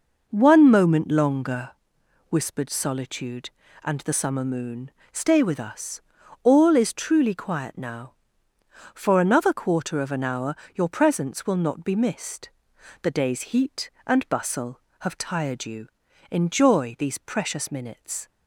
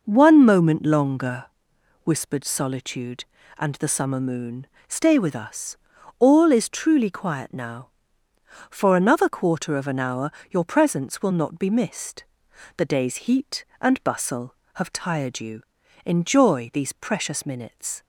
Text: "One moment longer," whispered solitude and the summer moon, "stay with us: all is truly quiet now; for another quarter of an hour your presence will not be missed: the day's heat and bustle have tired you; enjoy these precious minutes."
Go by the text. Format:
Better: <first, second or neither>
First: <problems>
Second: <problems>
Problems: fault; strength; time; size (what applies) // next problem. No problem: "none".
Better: neither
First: pauses between "hour" and "your"; slight; at 10.5 s; 0.18 s long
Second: pauses between "hour" and "your"; slight; at 10.3 s; 0.18 s long